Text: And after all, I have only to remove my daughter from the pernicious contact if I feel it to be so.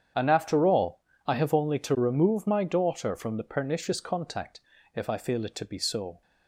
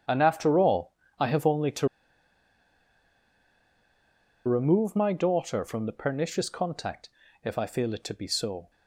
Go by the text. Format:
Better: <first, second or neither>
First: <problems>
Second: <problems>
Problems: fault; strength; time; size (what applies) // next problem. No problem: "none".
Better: first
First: starts louder than the rest; strong; until 1.4 s; 8.5 dB // pauses between "contact" and "if"; slight; at 4.5 s; 0.34 s long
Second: starts louder than the rest; strong; until 1.3 s; 8.5 dB // pauses between "to" and "remove"; strong; at 1.8 s; 2.5 s long // pauses between "contact" and "if"; slight; at 7.0 s; 0.34 s long